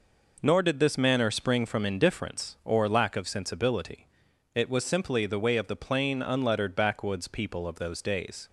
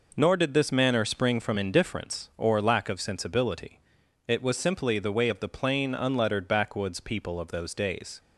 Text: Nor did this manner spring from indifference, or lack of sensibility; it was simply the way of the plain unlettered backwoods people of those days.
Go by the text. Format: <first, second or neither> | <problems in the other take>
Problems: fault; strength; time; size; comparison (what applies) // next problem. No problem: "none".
neither | none